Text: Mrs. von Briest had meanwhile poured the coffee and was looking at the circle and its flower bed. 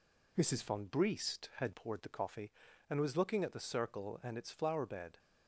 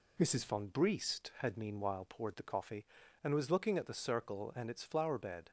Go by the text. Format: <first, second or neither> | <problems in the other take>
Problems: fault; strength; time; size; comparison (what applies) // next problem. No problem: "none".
second | skips "meanwhile"; at 1.7 s